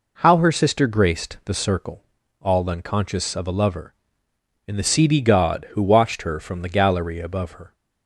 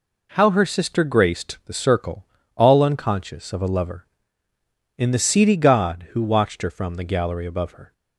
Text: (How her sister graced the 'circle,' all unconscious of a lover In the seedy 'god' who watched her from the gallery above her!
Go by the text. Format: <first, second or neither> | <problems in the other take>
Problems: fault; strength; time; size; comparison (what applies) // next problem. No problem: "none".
neither | none